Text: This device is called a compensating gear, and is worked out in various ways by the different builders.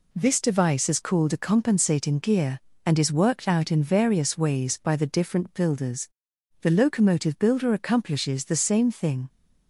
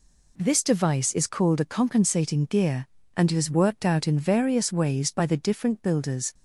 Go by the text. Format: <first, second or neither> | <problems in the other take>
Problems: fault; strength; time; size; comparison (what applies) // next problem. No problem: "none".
second | goes on to say "The locomotive builder accomplishes the same thing"; strong; from 6.6 s on; 2.6 s long